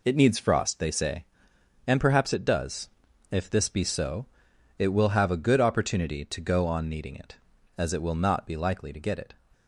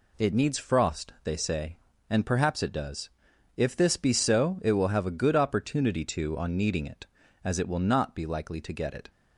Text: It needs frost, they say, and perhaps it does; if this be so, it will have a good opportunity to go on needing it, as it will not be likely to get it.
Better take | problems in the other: first | skips "go"; at 6.3 s

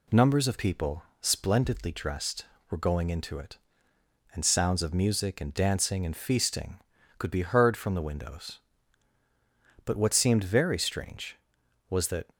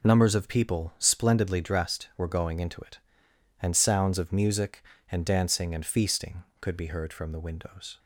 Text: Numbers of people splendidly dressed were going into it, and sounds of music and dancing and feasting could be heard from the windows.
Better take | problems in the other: second | pauses between "people" and "splendidly"; slight; at 1.0 s; 0.18 s long // goes on to say "But what seemed very strange was that"; strong; from 9.8 s on; 2.4 s long

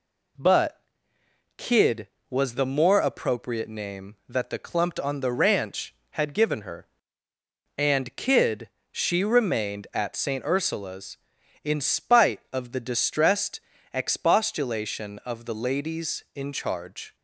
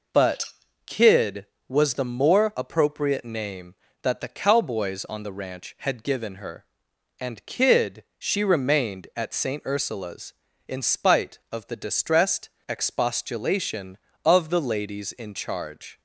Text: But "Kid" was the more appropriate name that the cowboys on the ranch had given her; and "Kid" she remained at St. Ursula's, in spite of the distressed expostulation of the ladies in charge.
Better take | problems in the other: second | pauses between "But" and "Kid"; noticeable; at 0.8 s; 0.76 s long; also in the second // says "clumped" for "cowboys"; at 4.5 s // pauses between "Kid" and "she"; slight; at 8.6 s; 0.24 s long // pauses between "distressed" and "expostulation"; slight; at 13.6 s; 0.32 s long; slight in the second

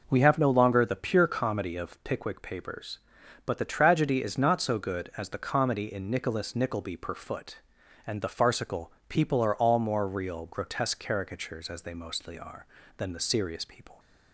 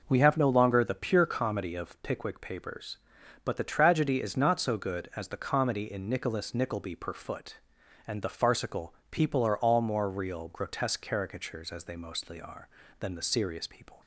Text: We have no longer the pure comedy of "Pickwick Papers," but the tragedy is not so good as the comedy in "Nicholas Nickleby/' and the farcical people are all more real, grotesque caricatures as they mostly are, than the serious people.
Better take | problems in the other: neither | pauses between "farcical" and "people"; slight; the same in both

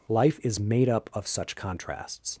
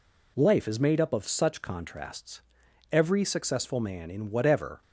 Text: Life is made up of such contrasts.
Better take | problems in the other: first | goes on to say "Every successful man in whatever"; strong; from 2.8 s on; 1.9 s long

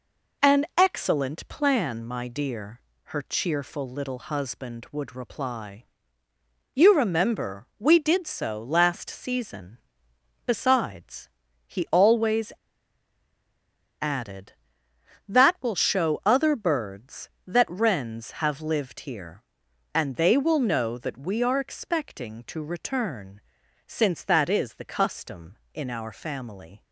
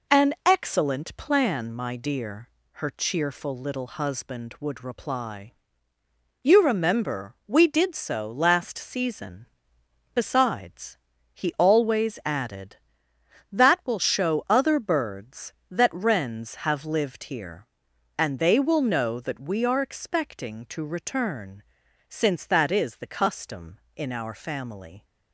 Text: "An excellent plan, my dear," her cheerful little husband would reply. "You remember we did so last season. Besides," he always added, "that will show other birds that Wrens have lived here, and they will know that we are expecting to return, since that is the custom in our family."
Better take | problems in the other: second | pauses between "always" and "added"; strong; at 12.5 s; 1.5 s long

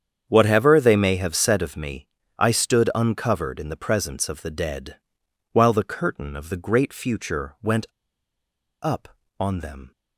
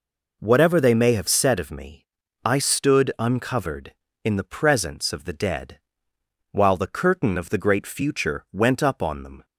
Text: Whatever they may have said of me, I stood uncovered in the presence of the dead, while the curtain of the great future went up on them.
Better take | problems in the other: second | starts louder than the rest; strong; until 1.2 s; 8 dB // pauses between "went" and "up"; noticeable; at 7.8 s; 0.95 s long

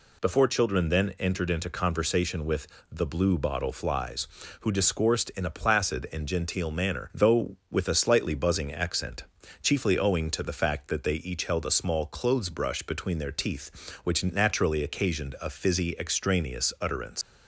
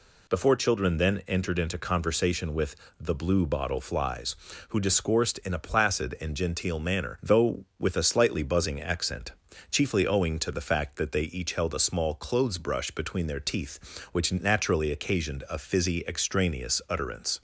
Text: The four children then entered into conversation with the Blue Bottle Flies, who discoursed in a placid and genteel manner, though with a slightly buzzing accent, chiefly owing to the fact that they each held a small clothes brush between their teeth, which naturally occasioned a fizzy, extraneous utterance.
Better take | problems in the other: second | pauses between "with" and "the"; slight; at 2.6 s; 0.24 s long; slight in the second // leaves "utterance" unfinished; at 17.2 s; 115 ms

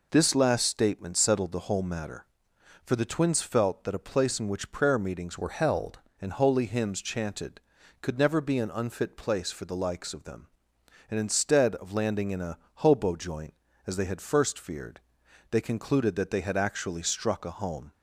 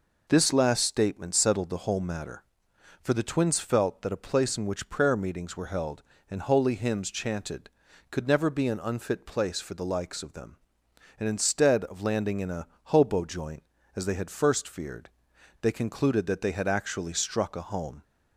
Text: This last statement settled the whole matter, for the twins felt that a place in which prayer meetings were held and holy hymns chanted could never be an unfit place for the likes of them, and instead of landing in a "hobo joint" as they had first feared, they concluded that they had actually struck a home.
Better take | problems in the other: second | changes voice from "were" to "held"; from 5.3 to 5.9 s; 0.6 s long // pauses between "a" and "hobo"; slight; at 12.5 s; 0.24 s long; slight in the second

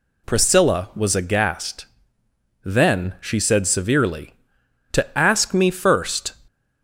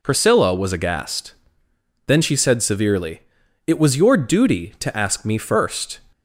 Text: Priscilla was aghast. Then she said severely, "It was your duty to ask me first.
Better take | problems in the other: second | skips "It was your duty"; at 4.6 s

